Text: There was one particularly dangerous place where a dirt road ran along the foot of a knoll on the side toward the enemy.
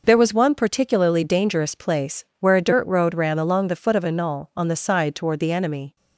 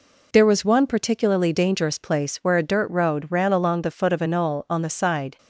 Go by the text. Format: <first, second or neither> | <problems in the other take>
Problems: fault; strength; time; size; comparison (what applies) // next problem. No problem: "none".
first | stops before "toward the enemy"; at 5.3 s